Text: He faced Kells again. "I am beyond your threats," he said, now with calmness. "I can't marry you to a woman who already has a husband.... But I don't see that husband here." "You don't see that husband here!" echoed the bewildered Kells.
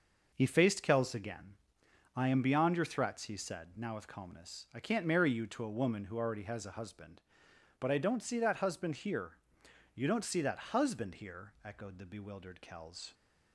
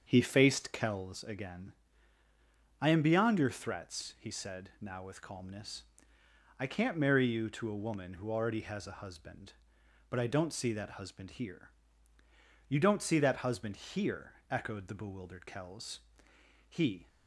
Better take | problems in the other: first | starts louder than the rest; until 1.0 s; 7 dB // goes on to say "He"; slight; from 16.6 s on; 0.38 s long

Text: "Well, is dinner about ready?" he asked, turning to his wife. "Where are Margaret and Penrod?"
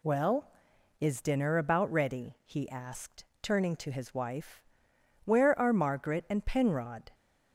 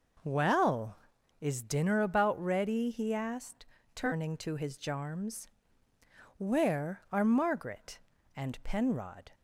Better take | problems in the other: first | says "jarms" for "wife"; at 4.7 s

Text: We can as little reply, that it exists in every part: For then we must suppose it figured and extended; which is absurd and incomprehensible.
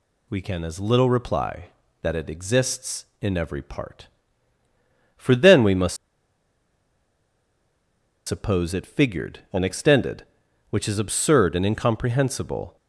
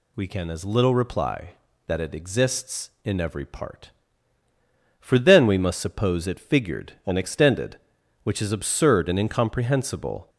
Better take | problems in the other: second | pauses between "must" and "suppose"; strong; at 5.9 s; 2.3 s long

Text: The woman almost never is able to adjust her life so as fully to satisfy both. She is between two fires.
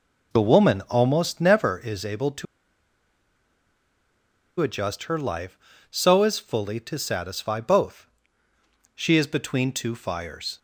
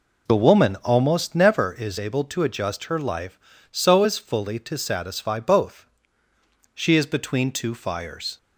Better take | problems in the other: second | pauses between "to" and "adjust"; strong; at 2.4 s; 2.1 s long

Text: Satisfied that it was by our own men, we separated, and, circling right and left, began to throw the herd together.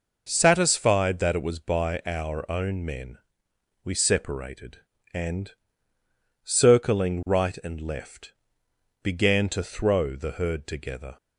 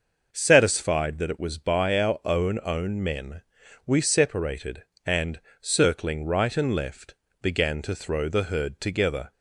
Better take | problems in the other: first | starts louder than the rest; noticeable; until 1.3 s; 6 dB // says "own" twice; at 2.6 s

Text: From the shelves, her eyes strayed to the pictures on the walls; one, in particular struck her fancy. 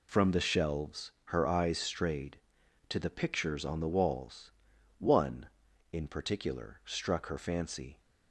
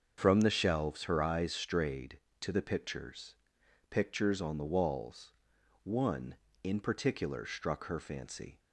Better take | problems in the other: first | starts louder than the rest; until 1.1 s; 6.5 dB // says "pictures" twice; at 3.8 s

